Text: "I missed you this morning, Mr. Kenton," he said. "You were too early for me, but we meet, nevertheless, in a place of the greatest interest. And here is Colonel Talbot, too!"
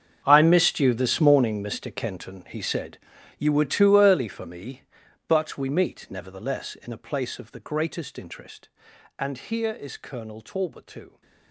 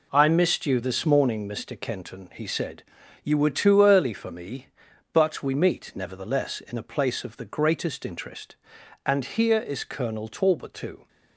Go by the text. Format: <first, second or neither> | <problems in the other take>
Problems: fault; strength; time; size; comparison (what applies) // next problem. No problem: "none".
second | gets quieter; strong; throughout; 17 dB